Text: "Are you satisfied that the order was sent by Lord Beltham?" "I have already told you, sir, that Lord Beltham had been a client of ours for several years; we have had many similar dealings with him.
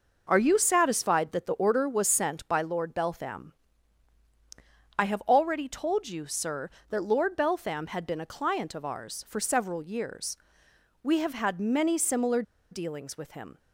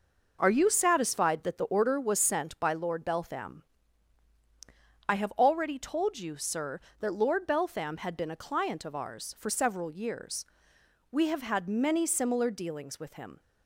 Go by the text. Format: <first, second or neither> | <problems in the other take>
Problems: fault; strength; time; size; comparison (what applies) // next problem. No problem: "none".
second | pauses between "similar" and "dealings"; slight; at 12.4 s; 0.29 s long